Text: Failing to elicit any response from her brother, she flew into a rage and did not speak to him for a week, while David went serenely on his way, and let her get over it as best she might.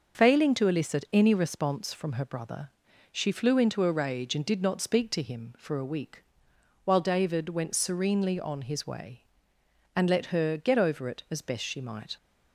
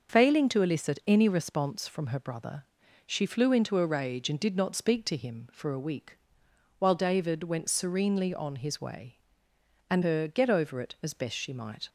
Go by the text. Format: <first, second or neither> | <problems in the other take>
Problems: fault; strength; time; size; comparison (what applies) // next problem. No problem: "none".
first | starts louder than the rest; until 1.1 s; 6 dB; noticeable in the first // skips "let"; at 10.0 s